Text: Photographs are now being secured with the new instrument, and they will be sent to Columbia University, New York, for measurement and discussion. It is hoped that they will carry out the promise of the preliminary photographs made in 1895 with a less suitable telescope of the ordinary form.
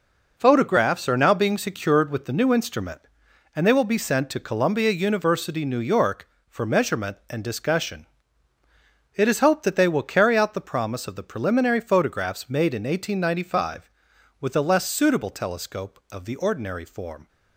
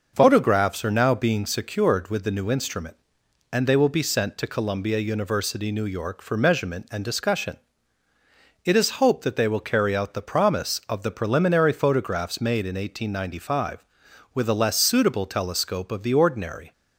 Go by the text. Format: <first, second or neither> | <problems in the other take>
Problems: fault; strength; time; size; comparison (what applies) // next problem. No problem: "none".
first | stops before "form"; at 16.7 s